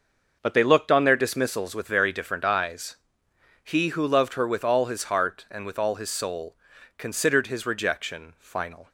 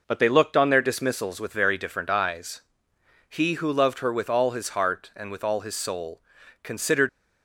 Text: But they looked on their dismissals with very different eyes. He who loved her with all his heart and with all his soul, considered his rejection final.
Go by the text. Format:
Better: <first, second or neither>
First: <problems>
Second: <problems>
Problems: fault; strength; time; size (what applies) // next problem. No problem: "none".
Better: first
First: none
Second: stops before "his rejection final"; at 7.0 s